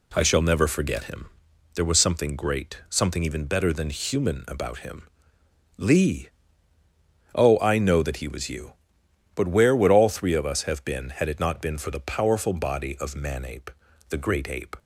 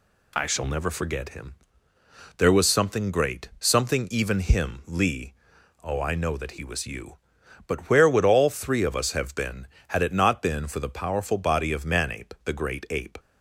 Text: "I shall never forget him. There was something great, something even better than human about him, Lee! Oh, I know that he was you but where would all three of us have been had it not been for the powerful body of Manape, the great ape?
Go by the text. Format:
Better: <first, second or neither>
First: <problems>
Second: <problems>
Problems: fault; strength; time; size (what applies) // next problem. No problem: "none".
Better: first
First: none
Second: skips "better than human about"; at 4.4 s